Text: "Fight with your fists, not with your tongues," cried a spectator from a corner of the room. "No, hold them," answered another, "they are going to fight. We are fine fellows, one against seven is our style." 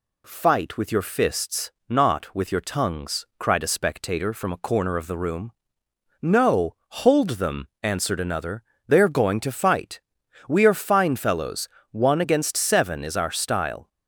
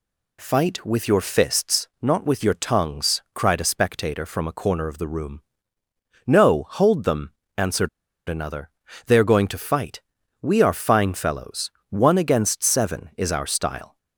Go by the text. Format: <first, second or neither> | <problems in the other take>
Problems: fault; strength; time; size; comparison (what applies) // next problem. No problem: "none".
first | pauses between "answered" and "another"; at 7.8 s; 0.40 s long